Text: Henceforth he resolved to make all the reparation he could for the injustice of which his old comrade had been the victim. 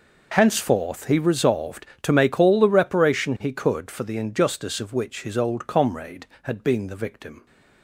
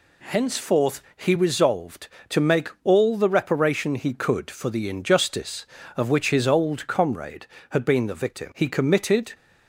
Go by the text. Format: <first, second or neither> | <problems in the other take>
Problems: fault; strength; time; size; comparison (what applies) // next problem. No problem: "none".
first | goes on to say "He committed"; noticeable; from 8.5 s on; 0.78 s long